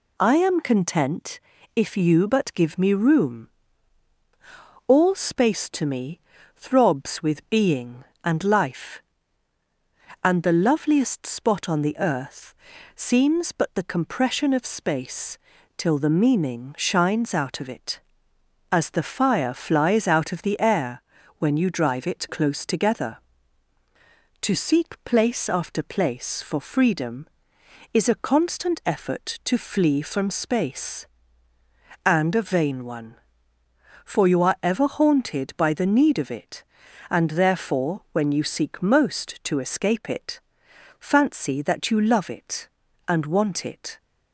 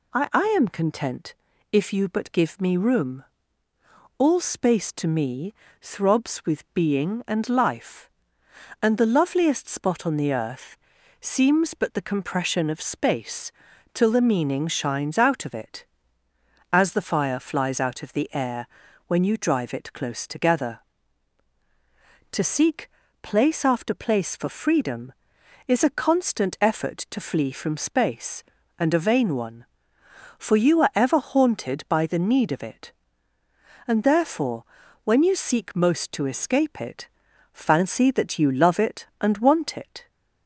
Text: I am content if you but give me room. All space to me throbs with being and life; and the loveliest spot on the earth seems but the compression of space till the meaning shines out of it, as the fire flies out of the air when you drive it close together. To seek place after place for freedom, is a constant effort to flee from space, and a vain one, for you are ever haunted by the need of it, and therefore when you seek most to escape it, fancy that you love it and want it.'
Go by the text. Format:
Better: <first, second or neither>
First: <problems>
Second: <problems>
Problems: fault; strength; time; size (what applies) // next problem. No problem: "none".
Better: first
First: pauses between "content" and "if"; slight; at 1.3 s; 0.36 s long // pauses between "me" and "throbs"; slight; at 6.2 s; 0.34 s long // pauses between "earth" and "seems"; at 12.5 s; 0.40 s long // pauses between "space" and "till"; at 15.3 s; 0.40 s long // pauses between "air" and "when"; slight; at 21.0 s; 0.34 s long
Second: says "I" twice; at 0.3 s // pauses between "content" and "if"; at 1.3 s; 0.38 s long // pauses between "me" and "throbs"; slight; at 5.5 s; 0.26 s long // pauses between "earth" and "seems"; at 10.7 s; 0.44 s long // pauses between "space" and "till"; at 13.5 s; 0.42 s long // pauses between "air" and "when"; at 18.6 s; 0.40 s long // pauses between "seek" and "place"; slight; at 22.8 s; 0.32 s long // pauses between "therefore" and "when"; at 34.6 s; 0.40 s long